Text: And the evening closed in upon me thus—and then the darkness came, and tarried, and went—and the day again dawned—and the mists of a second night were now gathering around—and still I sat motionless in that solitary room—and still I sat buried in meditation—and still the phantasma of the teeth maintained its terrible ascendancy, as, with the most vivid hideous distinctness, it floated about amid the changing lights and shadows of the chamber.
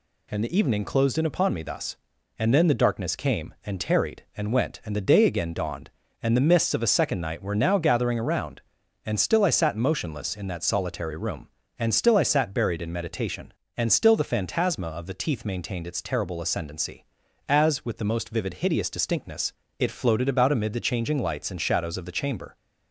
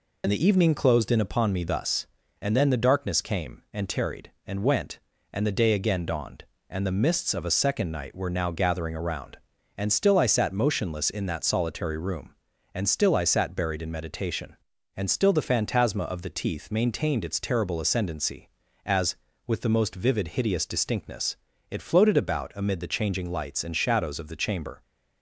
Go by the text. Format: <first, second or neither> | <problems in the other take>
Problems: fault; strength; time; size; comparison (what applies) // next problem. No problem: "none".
first | loses the start of "And"; at 0.2 s; 55 ms